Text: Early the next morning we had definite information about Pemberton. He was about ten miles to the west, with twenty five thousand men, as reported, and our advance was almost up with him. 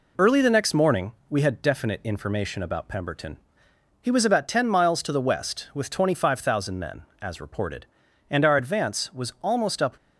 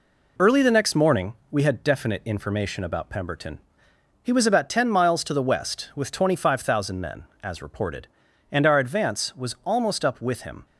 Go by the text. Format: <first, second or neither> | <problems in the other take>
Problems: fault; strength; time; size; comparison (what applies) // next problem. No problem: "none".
second | pauses between "morning" and "we"; slight; at 1.1 s; 0.18 s long; slight in the second // stops before "with him"; at 9.9 s